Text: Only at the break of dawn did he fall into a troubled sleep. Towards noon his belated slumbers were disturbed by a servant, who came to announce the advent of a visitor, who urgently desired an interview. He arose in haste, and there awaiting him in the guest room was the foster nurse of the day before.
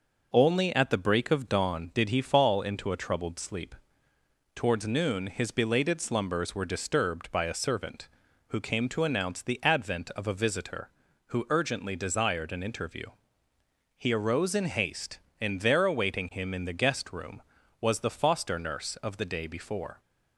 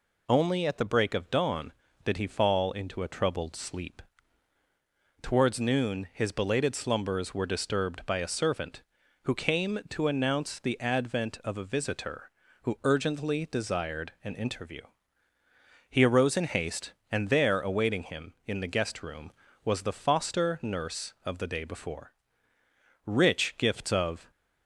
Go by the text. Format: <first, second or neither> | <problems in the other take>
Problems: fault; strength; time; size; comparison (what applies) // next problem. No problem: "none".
first | goes on to say "Rich gifts of"; noticeable; from 23.0 s on; 1.2 s long